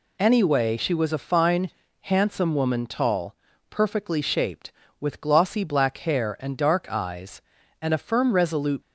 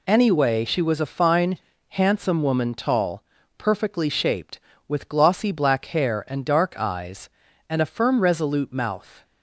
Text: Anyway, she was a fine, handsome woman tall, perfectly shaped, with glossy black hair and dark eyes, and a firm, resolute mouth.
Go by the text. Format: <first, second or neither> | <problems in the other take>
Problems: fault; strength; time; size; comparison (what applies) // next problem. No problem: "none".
second | stops before "mouth"; at 8.8 s